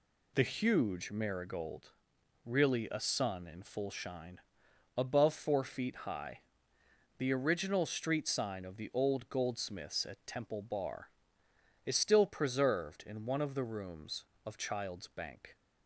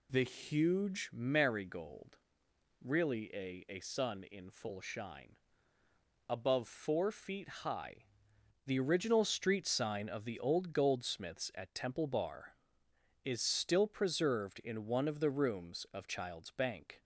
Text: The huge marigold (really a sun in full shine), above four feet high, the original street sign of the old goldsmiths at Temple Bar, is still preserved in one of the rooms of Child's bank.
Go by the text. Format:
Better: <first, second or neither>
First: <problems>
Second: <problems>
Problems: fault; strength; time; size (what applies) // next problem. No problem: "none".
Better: first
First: none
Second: says "a" twice; at 3.6 s // pauses between "feet" and "high"; slight; at 7.4 s; 0.16 s long